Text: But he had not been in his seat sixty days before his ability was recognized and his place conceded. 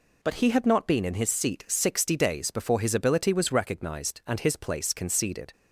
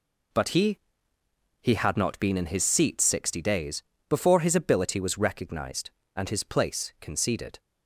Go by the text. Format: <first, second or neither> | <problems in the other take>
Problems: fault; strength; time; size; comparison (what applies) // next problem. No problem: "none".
first | says "he" twice; at 1.6 s // pauses between "days" and "before"; slight; at 3.8 s; 0.28 s long